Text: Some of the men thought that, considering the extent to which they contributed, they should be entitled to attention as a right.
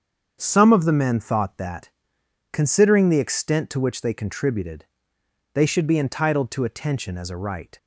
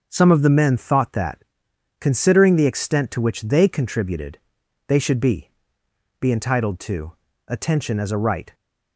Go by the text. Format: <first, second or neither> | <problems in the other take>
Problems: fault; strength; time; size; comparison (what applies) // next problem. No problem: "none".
first | starts louder than the rest; until 1.1 s; 6.5 dB; strong in the first // says "be" twice; at 6.1 s // pauses between "to" and "attention"; slight; at 7.1 s; 0.34 s long